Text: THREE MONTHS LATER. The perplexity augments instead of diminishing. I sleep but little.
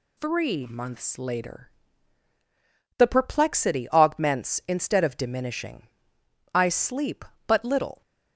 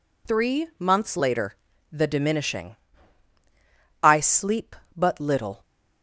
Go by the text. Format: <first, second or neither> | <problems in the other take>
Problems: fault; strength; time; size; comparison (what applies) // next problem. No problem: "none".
first | skips "perplexity augments instead of"; at 2.0 s